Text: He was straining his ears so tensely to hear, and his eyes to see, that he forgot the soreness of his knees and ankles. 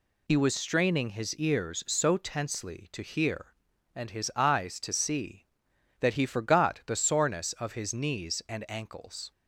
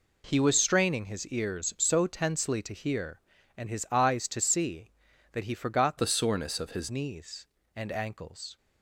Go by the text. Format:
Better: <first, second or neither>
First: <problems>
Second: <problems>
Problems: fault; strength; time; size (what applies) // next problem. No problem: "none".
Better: first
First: none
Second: changes voice from "the" to "his"; from 5.9 to 6.8 s; 0.9 s long